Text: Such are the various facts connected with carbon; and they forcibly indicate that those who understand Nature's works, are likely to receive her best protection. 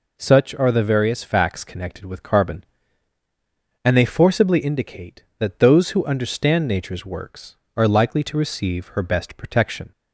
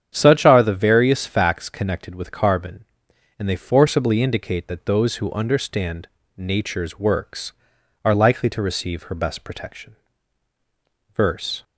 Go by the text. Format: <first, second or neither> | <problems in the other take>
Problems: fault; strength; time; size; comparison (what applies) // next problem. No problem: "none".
first | starts louder than the rest; strong; until 1.1 s; 8.5 dB // pauses between "understand" and "Nature's"; slight; at 6.0 s; 0.26 s long // goes on to say "Verse"; from 11.1 s on; 0.50 s long